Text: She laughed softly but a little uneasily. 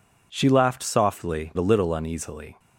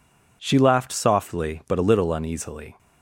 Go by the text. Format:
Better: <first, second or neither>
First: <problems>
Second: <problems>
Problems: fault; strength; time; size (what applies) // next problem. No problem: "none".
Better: second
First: skips "but"; at 1.5 s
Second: none